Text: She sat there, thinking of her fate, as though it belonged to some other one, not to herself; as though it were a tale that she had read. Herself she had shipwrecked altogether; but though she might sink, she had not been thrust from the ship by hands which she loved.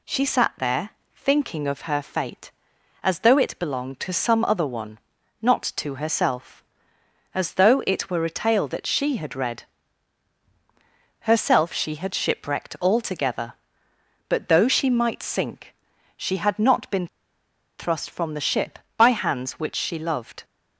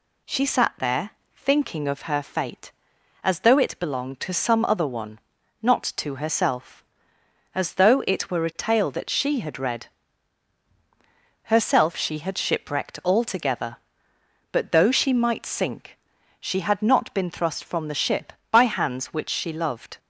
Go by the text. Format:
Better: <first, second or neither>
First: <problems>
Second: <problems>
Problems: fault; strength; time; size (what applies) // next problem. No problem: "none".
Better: second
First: pauses between "been" and "thrust"; noticeable; at 17.0 s; 0.71 s long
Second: none